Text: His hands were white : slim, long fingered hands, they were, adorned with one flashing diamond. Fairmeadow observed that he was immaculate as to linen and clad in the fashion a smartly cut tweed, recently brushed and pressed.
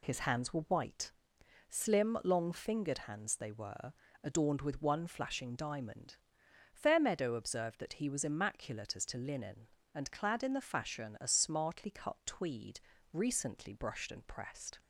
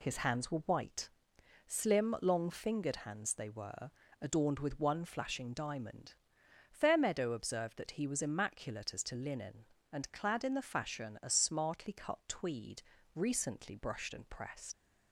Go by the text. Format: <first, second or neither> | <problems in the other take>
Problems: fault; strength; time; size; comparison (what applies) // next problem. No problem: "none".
first | leaves "pressed" unfinished; at 14.7 s; 85 ms